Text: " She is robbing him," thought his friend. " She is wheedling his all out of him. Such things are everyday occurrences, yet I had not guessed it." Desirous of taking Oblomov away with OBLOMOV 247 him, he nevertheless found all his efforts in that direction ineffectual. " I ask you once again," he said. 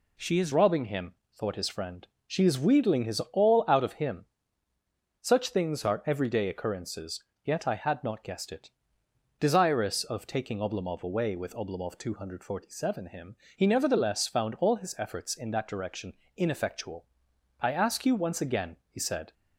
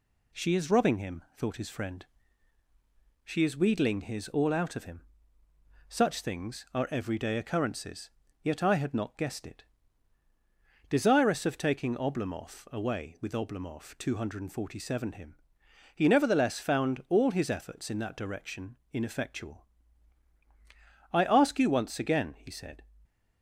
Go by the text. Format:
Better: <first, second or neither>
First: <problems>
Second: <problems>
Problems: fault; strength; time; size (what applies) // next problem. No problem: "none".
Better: second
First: changes voice at "robbing"; from 0.5 s on; 18.8 s long // pauses between "direction" and "ineffectual"; slight; at 16.1 s; 0.24 s long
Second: pauses between "direction" and "ineffectual"; slight; at 18.7 s; 0.16 s long